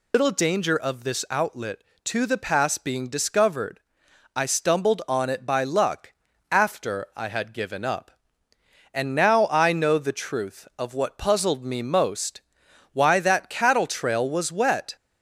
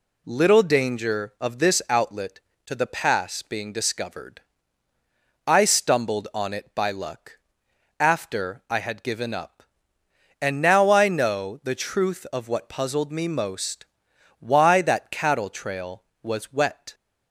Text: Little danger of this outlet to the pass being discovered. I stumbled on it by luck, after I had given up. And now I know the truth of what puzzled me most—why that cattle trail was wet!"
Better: second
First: loses the start of "Little"; at 0.1 s; 140 ms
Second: none

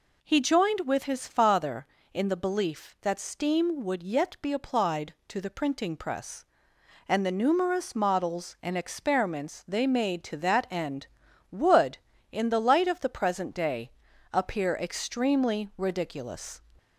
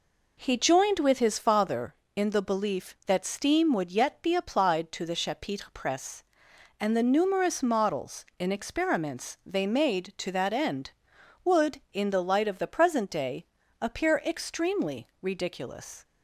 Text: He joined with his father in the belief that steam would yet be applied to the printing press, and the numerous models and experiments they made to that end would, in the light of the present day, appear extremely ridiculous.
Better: first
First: none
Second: says "chapitre" for "printing"; at 5.1 s

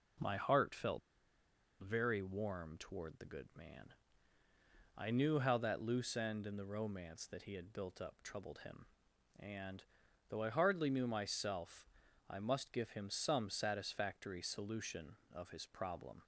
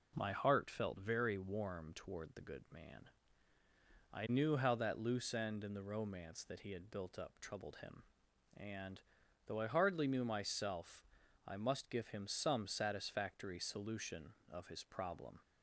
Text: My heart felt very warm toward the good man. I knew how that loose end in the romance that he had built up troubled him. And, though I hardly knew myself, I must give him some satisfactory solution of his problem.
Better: second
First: pauses between "felt" and "very"; noticeable; at 1.0 s; 0.82 s long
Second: none

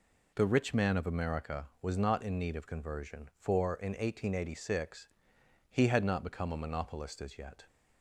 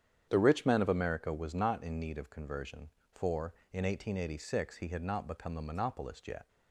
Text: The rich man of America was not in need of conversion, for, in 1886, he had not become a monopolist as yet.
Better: first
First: none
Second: starts louder than the rest; strong; until 1.3 s; 8.5 dB // skips "as"; at 6.2 s

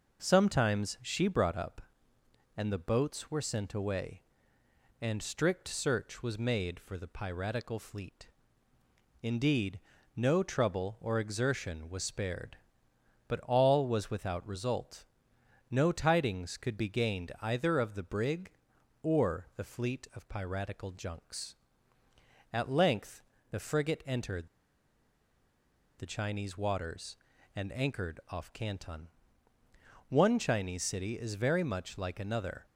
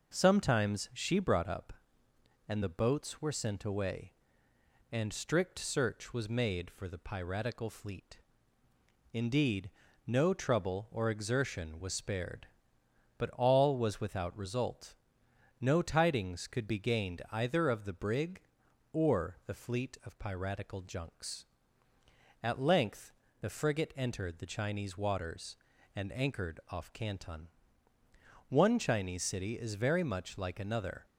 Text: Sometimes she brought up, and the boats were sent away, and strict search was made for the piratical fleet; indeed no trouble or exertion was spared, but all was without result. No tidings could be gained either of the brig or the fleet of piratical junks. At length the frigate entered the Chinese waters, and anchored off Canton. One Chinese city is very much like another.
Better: second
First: pauses between "indeed" and "no"; slight; at 9.7 s; 0.36 s long // pauses between "length" and "the"; slight; at 23.2 s; 0.26 s long // pauses between "entered" and "the"; strong; at 24.4 s; 1.5 s long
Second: pauses between "indeed" and "no"; slight; at 9.6 s; 0.36 s long // pauses between "length" and "the"; slight; at 23.1 s; 0.26 s long

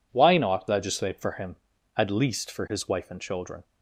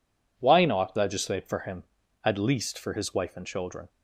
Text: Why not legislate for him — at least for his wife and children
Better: neither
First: none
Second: none

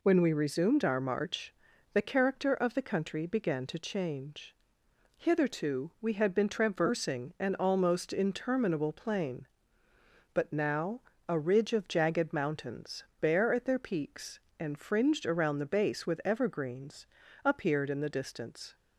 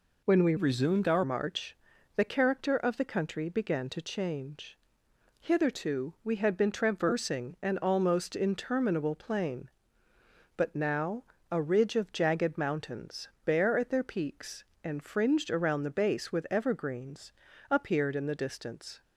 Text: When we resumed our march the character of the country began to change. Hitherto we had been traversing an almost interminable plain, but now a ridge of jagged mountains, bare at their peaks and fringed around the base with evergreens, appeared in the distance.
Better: first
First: pauses between "march" and "the"; at 1.5 s; 0.40 s long // pauses between "now" and "a"; slight; at 11.0 s; 0.28 s long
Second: changes voice from "resumed" to "our"; from 0.5 to 1.2 s; 0.7 s long // pauses between "march" and "the"; at 1.7 s; 0.40 s long // pauses between "now" and "a"; slight; at 11.2 s; 0.28 s long

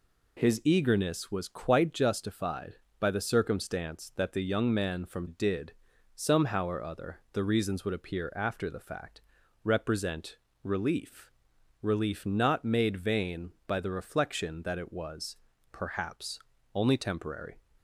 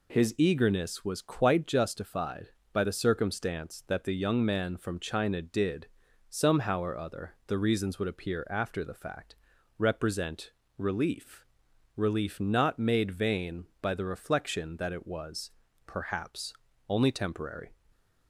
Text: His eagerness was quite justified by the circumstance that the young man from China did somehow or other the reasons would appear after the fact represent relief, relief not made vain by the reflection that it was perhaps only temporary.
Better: second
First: skips "China"; at 5.2 s // pauses between "did" and "somehow"; noticeable; at 5.7 s; 0.46 s long // pauses between "fact" and "represent"; at 9.2 s; 0.42 s long // pauses between "represent" and "relief"; slight; at 10.3 s; 0.30 s long // pauses between "was" and "perhaps"; slight; at 15.3 s; 0.34 s long // pauses between "perhaps" and "only"; slight; at 16.3 s; 0.34 s long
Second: pauses between "did" and "somehow"; noticeable; at 5.8 s; 0.46 s long // pauses between "fact" and "represent"; at 9.3 s; 0.42 s long // pauses between "represent" and "relief"; slight; at 10.4 s; 0.30 s long // pauses between "was" and "perhaps"; slight; at 15.5 s; 0.34 s long // pauses between "perhaps" and "only"; slight; at 16.5 s; 0.34 s long

